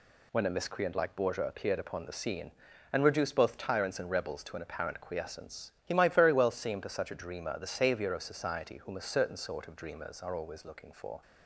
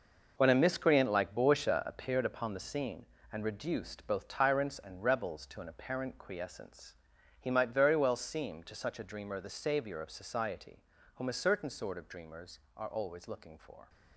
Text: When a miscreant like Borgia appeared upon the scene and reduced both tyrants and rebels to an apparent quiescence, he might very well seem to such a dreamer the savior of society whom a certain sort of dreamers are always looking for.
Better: first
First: none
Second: gets quieter; strong; throughout; 10.5 dB // pauses between "society" and "whom"; slight; at 10.8 s; 0.32 s long

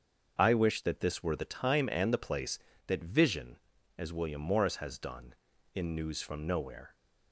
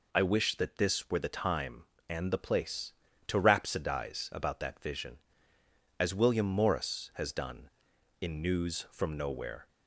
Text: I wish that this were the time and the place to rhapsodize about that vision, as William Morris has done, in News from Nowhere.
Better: second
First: starts louder than the rest; until 1.4 s; 6.5 dB // skips "to rhapsodize about"; at 2.7 s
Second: none

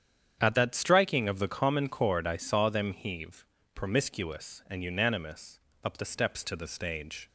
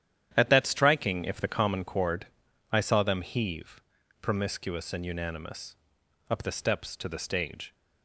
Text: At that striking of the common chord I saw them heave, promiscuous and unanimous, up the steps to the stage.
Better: first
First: starts louder than the rest; strong; until 1.4 s; 8.5 dB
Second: starts louder than the rest; strong; until 1.3 s; 10 dB // says "if" for "of"; at 1.2 s // pauses between "chord" and "I"; at 2.2 s; 0.44 s long

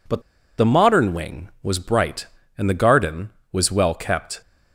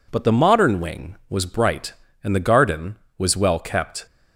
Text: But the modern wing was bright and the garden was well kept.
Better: second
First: pauses between "But" and "the"; at 0.2 s; 0.37 s long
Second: none

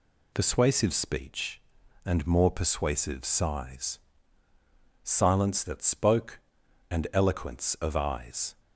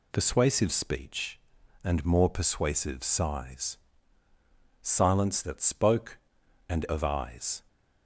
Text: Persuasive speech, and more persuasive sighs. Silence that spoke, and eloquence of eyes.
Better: first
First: none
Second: skips "eloquence"; at 6.8 s

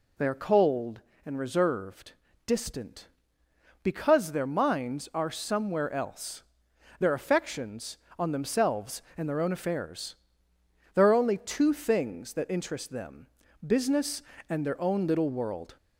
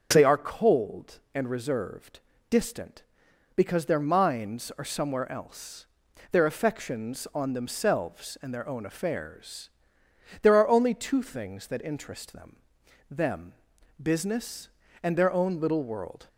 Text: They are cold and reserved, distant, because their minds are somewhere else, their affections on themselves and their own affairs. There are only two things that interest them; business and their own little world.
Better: first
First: none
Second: starts louder than the rest; until 1.1 s; 6.5 dB // says "them" twice; at 13.0 s

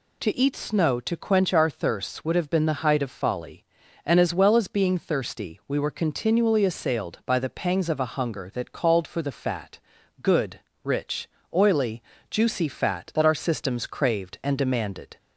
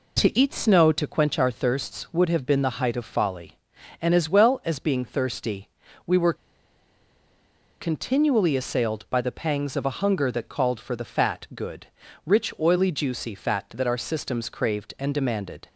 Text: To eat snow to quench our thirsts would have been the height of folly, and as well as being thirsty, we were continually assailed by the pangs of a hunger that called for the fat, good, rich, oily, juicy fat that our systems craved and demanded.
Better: first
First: none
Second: pauses between "were" and "continually"; strong; at 6.3 s; 1.4 s long

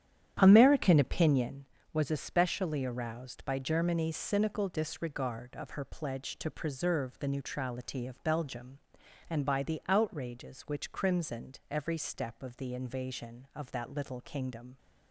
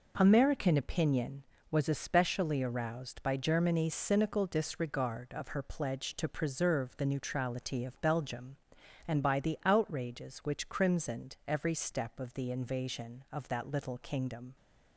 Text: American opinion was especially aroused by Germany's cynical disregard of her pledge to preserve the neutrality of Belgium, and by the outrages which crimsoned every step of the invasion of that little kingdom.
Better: second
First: starts louder than the rest; strong; until 1.5 s; 9.5 dB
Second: none

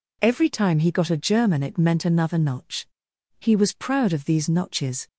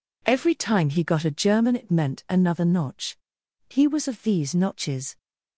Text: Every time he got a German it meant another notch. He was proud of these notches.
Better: first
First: none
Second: skips "proud"; at 4.0 s

